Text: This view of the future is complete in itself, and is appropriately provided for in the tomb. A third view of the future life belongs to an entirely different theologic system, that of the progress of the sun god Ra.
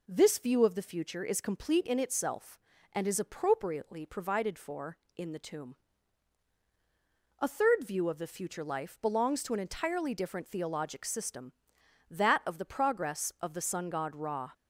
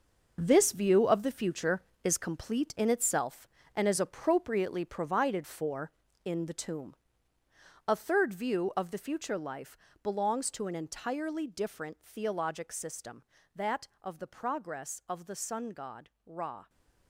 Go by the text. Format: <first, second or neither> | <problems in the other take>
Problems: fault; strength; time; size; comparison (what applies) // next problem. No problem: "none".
first | gets quieter; strong; throughout; 10 dB // pauses between "life" and "belongs"; slight; at 9.7 s; 0.26 s long // pauses between "god" and "Ra"; slight; at 16.0 s; 0.16 s long